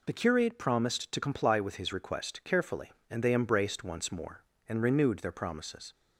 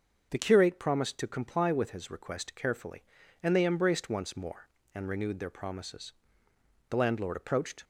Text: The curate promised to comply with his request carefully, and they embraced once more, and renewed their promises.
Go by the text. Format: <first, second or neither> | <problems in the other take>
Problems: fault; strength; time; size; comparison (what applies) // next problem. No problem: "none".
first | starts louder than the rest; until 1.3 s; 6.5 dB // goes on to say "The landlord approached"; noticeable; from 6.8 s on; 0.94 s long